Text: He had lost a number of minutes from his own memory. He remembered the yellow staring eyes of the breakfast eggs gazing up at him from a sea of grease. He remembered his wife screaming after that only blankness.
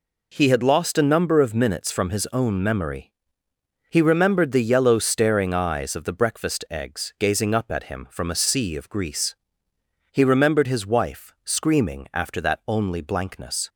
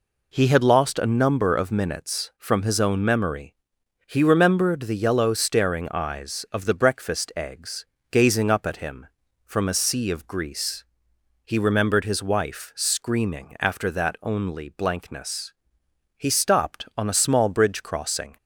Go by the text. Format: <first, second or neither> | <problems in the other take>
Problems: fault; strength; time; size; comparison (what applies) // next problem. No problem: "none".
first | pauses between "eggs" and "gazing"; slight; at 7.8 s; 0.26 s long // goes on to say "He stopped on a small bridge crossing"; strong; from 16.1 s on; 2.2 s long